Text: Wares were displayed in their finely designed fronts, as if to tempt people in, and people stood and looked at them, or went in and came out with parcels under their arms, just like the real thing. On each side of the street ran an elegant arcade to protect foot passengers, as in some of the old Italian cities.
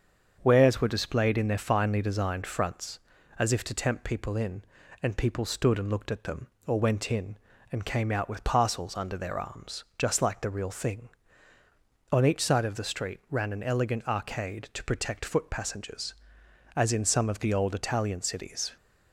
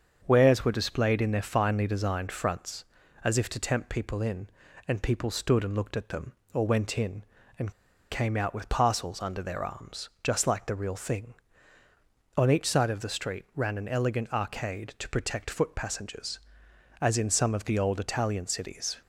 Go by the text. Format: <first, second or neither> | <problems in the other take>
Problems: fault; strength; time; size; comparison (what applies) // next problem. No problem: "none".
first | starts louder than the rest; until 1.2 s; 7 dB; also in the first // pauses between "and" and "came"; at 7.7 s; 0.38 s long